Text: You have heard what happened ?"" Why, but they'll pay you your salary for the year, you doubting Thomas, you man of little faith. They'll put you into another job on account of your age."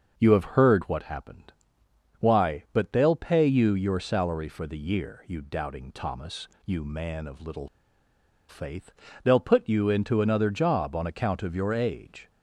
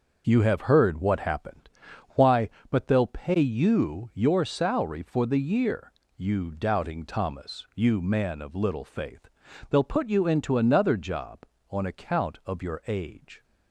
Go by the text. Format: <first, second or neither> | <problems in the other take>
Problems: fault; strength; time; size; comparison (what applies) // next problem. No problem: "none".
second | starts louder than the rest; until 1.1 s; 6.5 dB; noticeable in the second // pauses between "little" and "faith"; noticeable; at 7.6 s; 0.81 s long